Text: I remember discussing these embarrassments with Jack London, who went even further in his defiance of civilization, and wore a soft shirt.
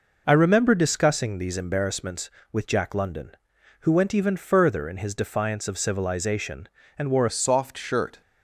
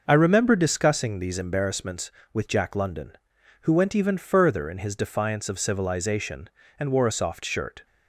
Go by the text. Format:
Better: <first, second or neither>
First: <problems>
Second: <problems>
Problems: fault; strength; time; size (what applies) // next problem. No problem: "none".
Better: second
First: changes voice at "a"; from 7.2 s on; 1.0 s long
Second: none